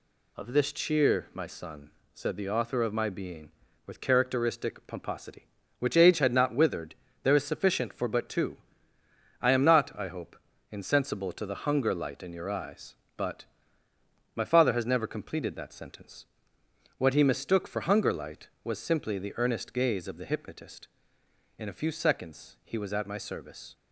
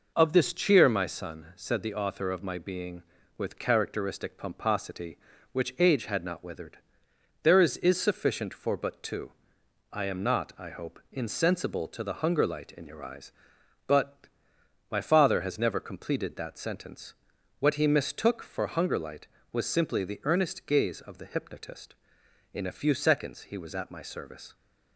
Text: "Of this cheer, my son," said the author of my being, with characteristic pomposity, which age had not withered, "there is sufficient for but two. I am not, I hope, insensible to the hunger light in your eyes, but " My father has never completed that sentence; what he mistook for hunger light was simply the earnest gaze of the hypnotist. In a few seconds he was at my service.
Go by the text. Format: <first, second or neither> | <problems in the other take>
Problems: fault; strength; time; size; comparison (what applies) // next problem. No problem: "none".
first | says "is" twice; at 7.7 s